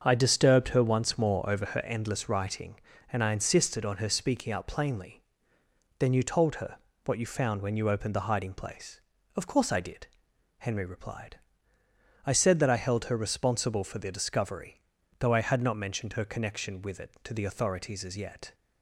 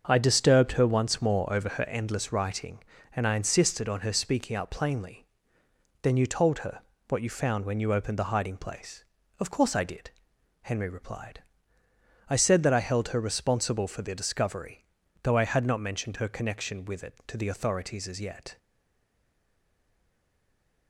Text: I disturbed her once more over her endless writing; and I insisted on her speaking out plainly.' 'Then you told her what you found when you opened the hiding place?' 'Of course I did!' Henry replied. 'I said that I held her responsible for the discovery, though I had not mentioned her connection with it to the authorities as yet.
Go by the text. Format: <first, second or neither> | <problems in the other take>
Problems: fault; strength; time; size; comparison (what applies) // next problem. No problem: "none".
first | starts louder than the rest; until 1.0 s; 6.5 dB; also in the first // pauses between "her" and "what"; slight; at 6.8 s; 0.26 s long; slight in the first // stays silent after the last word; from 18.5 s on; 2.3 s long